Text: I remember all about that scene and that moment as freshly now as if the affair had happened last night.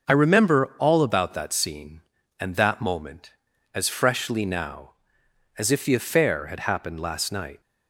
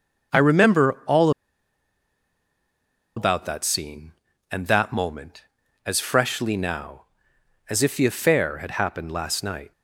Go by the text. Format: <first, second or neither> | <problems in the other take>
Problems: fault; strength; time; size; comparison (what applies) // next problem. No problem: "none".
first | pauses between "all" and "about"; strong; at 1.2 s; 1.8 s long